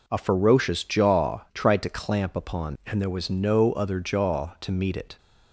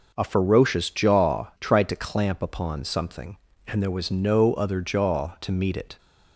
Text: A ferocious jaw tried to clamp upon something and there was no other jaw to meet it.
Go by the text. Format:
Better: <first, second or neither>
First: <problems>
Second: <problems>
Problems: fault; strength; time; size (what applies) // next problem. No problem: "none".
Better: second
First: skips "something"; at 2.8 s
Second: none